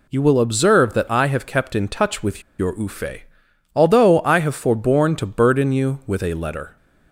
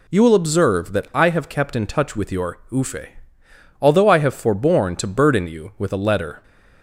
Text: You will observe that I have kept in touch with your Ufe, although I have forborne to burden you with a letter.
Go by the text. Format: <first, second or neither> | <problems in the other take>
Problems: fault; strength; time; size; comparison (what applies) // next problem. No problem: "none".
second | pauses between "with" and "your"; slight; at 2.4 s; 0.17 s long